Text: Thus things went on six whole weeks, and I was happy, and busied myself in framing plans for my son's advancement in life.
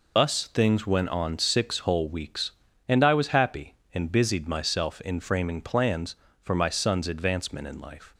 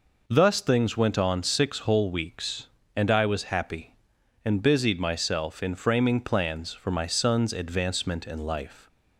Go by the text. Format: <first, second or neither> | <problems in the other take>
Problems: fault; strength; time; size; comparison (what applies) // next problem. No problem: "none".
second | loses the start of "Thus"; at 0.1 s; 80 ms